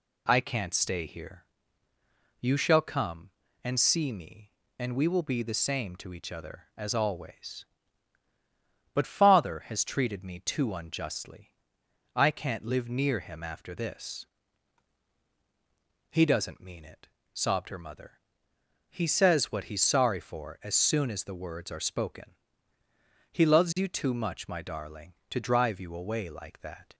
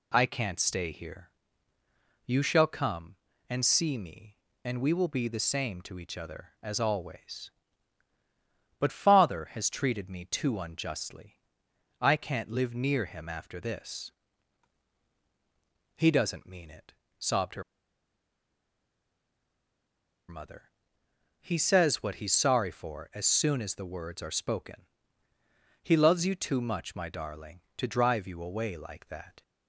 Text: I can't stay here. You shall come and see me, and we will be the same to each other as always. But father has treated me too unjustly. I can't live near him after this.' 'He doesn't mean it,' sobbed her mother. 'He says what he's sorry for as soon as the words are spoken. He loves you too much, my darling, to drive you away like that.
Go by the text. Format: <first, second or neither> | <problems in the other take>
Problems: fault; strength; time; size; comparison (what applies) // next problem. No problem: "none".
first | pauses between "her" and "mother"; strong; at 17.6 s; 2.6 s long